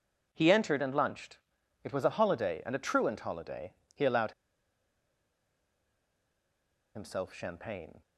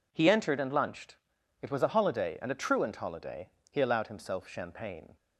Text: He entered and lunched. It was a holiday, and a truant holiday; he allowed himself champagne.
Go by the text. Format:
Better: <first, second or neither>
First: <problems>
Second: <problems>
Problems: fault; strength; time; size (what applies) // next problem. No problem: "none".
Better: second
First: pauses between "allowed" and "himself"; strong; at 4.3 s; 2.6 s long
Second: none